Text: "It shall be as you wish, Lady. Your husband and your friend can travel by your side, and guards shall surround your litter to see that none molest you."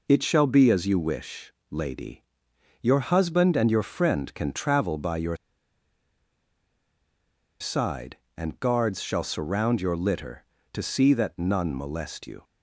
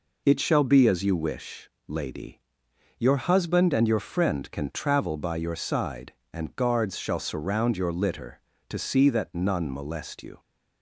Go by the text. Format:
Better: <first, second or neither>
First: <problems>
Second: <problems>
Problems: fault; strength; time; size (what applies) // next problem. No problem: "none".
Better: second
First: pauses between "your" and "side"; strong; at 5.3 s; 2.2 s long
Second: none